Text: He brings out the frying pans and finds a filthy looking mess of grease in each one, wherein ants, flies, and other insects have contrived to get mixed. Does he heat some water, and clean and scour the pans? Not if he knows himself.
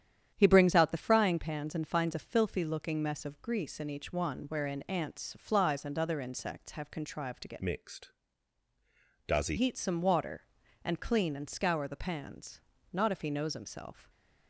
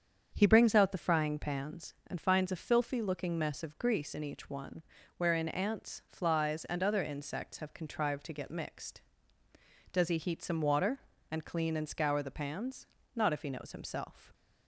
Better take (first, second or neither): second